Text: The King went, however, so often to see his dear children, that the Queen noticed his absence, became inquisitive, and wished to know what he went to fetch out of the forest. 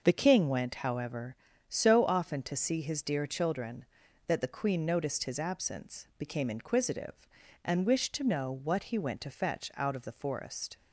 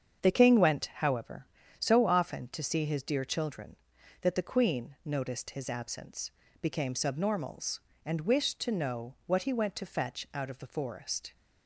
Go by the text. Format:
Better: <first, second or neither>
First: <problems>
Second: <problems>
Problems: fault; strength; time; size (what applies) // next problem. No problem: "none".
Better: first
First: none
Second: starts louder than the rest; strong; until 1.3 s; 7.5 dB // says "subnormals" for "inquisitive"; at 6.9 s